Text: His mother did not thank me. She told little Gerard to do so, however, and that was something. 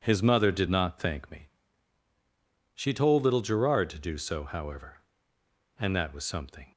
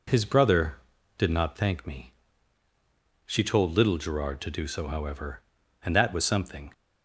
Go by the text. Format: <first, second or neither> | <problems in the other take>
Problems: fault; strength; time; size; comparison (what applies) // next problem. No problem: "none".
first | says "brother" for "mother"; at 0.2 s